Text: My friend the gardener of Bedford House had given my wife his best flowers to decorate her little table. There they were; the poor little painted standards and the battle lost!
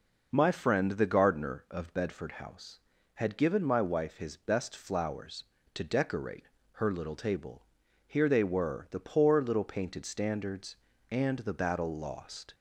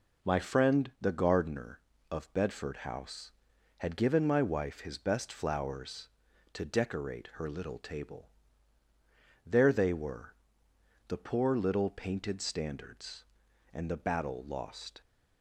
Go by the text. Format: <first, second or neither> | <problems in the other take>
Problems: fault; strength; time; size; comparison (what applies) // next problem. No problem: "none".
second | pauses between "decorate" and "her"; slight; at 6.4 s; 0.22 s long // says "Here" for "There"; at 8.0 s